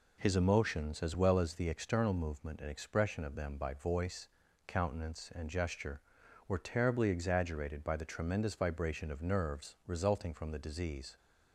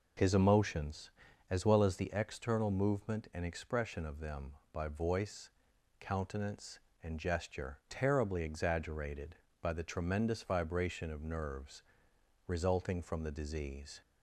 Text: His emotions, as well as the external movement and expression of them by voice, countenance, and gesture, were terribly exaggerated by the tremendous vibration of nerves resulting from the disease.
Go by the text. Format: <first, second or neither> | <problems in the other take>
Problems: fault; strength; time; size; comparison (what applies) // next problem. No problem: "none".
first | skips "were"; at 7.8 s // pauses between "nerves" and "resulting"; noticeable; at 11.8 s; 0.66 s long